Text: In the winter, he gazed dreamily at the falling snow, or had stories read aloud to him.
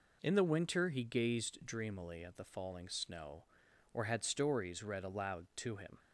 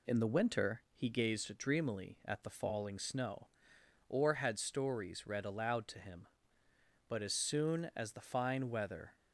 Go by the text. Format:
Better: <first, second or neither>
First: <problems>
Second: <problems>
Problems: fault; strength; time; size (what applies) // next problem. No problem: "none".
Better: first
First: none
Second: goes on to say "But as soon as the fine weather"; strong; from 7.0 s on; 2.0 s long